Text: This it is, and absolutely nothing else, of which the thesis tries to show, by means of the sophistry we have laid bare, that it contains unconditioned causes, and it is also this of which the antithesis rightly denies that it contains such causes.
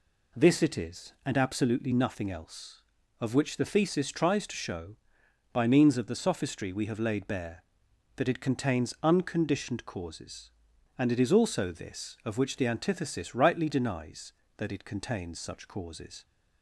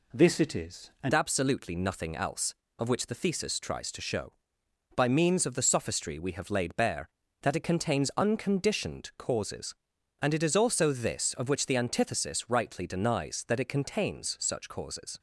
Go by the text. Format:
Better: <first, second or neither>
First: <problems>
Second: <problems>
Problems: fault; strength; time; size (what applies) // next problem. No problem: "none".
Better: first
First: none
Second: changes voice at "absolutely"; from 1.1 s on; 14.0 s long